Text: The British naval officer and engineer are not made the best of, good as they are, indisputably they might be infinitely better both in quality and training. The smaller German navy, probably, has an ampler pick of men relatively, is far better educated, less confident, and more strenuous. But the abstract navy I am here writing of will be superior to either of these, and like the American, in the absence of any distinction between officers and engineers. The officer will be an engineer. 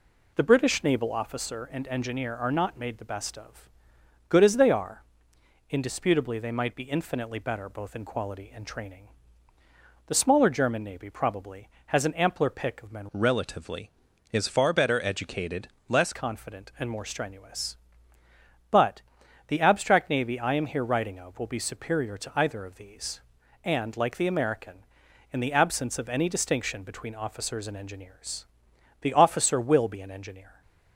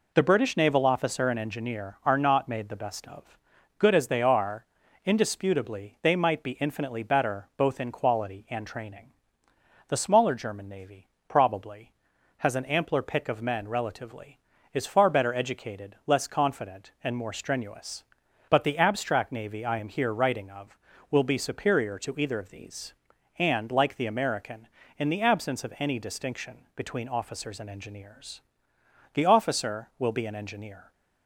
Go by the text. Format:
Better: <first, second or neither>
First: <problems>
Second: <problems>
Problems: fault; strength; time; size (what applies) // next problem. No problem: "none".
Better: second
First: changes voice from "relatively" to "less"; from 13.1 to 16.1 s; 3.0 s long // pauses between "But" and "the"; noticeable; at 19.0 s; 0.48 s long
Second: none